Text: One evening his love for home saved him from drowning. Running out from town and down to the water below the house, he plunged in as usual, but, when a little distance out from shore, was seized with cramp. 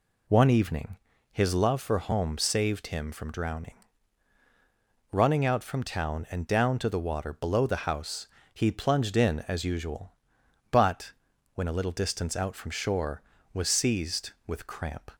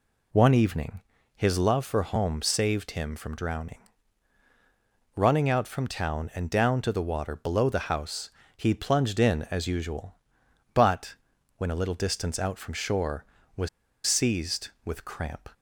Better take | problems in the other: first | pauses between "evening" and "his"; slight; at 1.0 s; 0.34 s long; slight in the first // pauses between "was" and "seized"; at 13.6 s; 0.38 s long

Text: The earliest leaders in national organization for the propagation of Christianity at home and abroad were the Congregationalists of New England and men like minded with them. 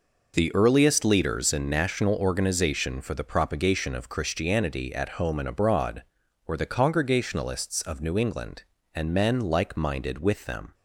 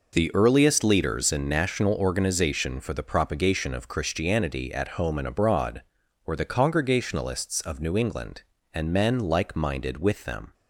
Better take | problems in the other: neither | none

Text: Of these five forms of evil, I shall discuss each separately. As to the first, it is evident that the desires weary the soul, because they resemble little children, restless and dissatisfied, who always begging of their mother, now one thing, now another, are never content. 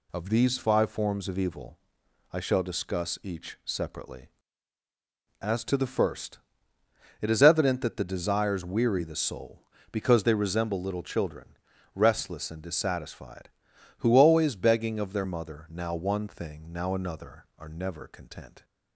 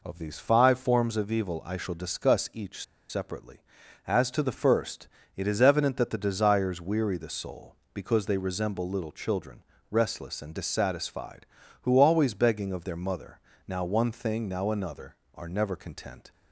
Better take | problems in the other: first | pauses between "each" and "separately"; slight; at 2.8 s; 0.26 s long

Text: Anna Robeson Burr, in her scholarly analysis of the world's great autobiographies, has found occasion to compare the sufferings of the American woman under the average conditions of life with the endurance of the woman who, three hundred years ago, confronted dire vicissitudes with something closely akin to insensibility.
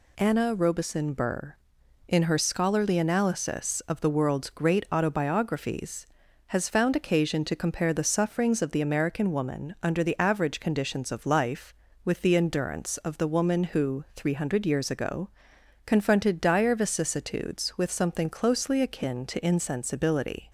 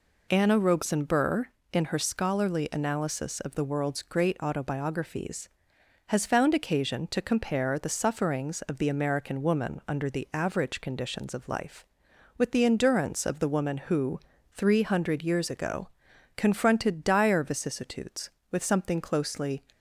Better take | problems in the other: first | stops before "akin to insensibility"; at 19.7 s

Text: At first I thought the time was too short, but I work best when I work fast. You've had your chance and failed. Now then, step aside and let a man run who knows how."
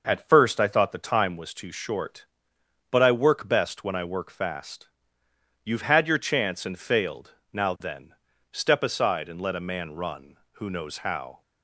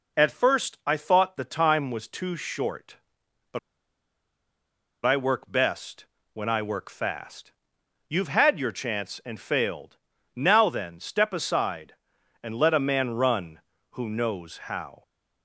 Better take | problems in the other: first | pauses between "but" and "I"; strong; at 3.5 s; 1.4 s long // pauses between "best" and "when"; slight; at 6.0 s; 0.28 s long

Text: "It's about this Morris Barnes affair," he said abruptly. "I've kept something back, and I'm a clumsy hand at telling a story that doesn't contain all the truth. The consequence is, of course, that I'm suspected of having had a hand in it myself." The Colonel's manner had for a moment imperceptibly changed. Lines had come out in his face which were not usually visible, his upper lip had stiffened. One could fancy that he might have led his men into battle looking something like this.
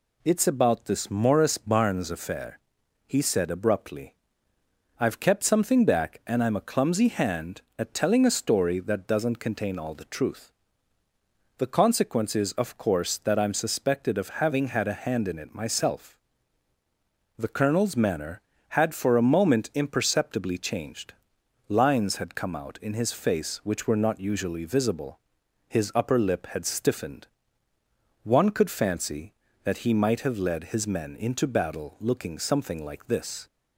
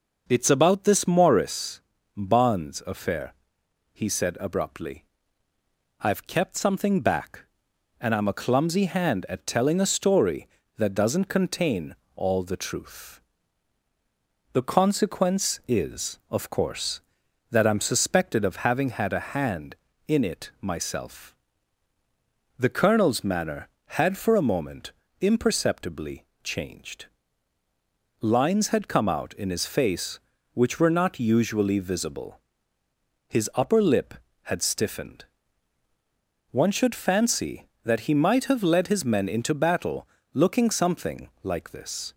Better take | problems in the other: first | pauses between "Morris" and "Barnes"; slight; at 1.8 s; 0.36 s long // pauses between "contain" and "all"; slight; at 11.9 s; 0.22 s long // pauses between "moment" and "imperceptibly"; slight; at 24.9 s; 0.30 s long // pauses between "imperceptibly" and "changed"; slight; at 26.2 s; 0.18 s long // says "should" for "could"; at 36.7 s // pauses between "battle" and "looking"; slight; at 40.0 s; 0.24 s long

